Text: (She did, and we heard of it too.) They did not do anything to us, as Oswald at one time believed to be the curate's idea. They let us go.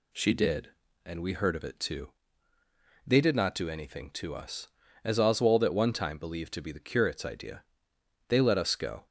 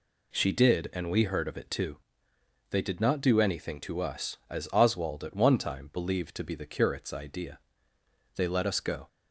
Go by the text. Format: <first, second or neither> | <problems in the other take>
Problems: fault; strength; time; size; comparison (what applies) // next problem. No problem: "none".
neither | none